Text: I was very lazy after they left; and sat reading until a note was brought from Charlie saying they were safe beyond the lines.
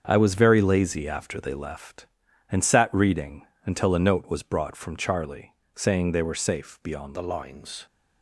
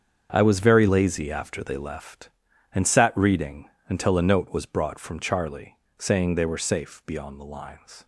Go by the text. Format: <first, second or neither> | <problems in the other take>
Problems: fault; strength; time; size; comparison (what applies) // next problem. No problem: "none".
second | starts louder than the rest; until 1.0 s; 7 dB; strong in the second // pauses between "reading" and "until"; slight; at 3.4 s; 0.20 s long; slight in the second // pauses between "Charlie" and "saying"; slight; at 5.5 s; 0.18 s long; slight in the second // changes voice at "the"; from 7.1 s on; 0.7 s long